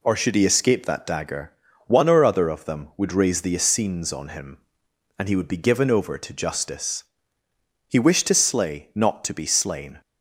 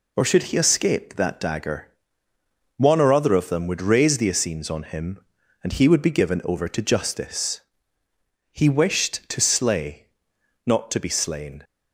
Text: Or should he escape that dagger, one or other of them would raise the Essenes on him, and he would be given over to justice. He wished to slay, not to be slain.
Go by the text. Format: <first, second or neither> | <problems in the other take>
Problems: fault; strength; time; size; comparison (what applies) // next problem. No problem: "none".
neither | none